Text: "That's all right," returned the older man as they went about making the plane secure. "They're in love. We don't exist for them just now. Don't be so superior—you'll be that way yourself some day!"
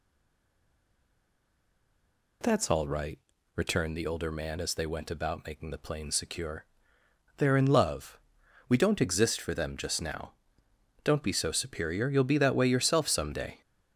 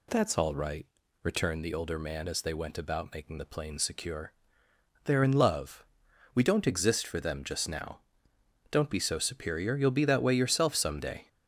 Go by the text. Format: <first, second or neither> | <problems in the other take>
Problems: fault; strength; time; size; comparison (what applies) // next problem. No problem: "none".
second | stays silent before the first word; until 2.4 s; 2.4 s long